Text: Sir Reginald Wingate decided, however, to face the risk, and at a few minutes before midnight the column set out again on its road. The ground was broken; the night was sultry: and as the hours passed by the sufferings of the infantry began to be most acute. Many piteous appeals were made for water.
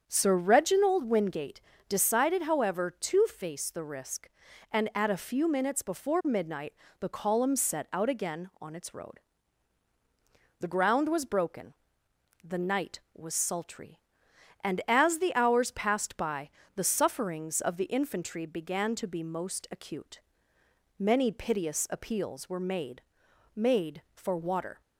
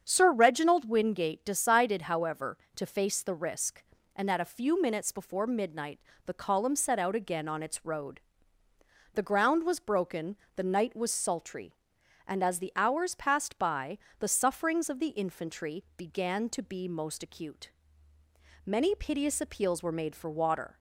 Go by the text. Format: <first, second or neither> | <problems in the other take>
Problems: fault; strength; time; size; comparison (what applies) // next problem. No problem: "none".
second | starts louder than the rest; strong; until 1.0 s; 7 dB; strong in the second // pauses between "Wingate" and "decided"; slight; at 1.6 s; 0.28 s long // pauses between "midnight" and "the"; slight; at 6.7 s; 0.28 s long; slight in the second // pauses between "by" and "the"; slight; at 16.4 s; 0.26 s long; slight in the second // says "made" twice; at 23.5 s